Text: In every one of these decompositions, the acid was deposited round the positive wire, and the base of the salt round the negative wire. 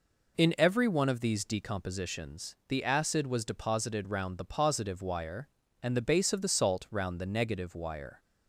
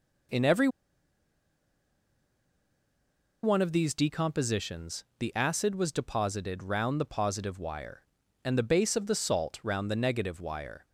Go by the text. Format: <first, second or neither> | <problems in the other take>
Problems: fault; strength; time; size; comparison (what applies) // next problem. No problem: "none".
first | pauses between "every" and "one"; strong; at 0.6 s; 2.7 s long